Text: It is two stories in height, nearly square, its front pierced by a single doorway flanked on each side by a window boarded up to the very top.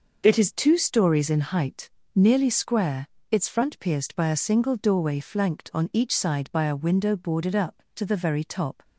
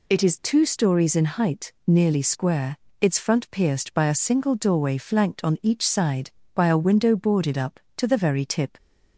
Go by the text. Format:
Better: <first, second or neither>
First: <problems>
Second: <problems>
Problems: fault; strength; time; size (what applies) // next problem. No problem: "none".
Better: first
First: none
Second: says "tip" for "top"; at 8.4 s